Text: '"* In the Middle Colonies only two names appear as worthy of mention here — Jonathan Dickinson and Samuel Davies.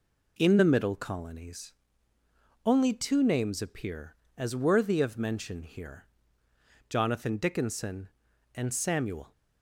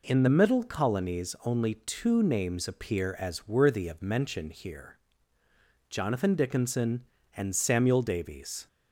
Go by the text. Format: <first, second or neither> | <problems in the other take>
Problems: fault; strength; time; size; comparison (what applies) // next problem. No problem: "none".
second | pauses between "Colonies" and "only"; noticeable; at 1.7 s; 0.94 s long // stops before "Davies"; at 9.3 s